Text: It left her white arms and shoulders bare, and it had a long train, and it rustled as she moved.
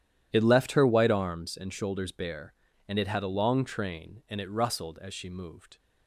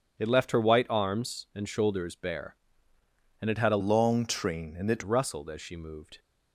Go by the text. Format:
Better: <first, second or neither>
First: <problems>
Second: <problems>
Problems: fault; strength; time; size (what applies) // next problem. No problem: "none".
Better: first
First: none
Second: changes voice from "long" to "it"; from 3.7 to 5.0 s; 1.3 s long